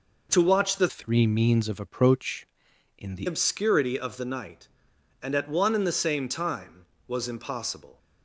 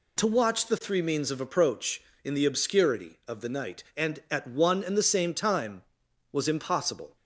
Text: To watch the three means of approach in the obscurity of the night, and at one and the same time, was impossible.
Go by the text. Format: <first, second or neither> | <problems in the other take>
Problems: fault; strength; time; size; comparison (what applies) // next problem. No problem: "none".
second | changes voice from "three" to "the"; from 0.8 to 3.2 s; 2.4 s long